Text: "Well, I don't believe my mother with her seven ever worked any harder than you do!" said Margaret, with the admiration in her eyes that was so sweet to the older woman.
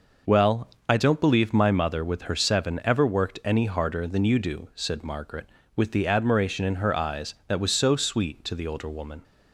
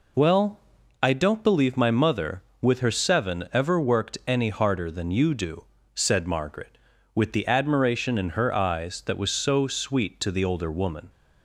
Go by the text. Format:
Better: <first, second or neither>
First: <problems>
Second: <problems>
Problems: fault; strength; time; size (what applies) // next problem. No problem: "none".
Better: neither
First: none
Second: none